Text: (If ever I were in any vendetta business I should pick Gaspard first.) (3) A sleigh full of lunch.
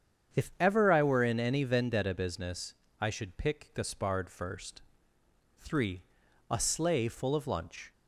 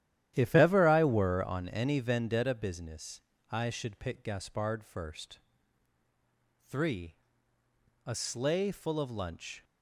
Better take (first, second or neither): first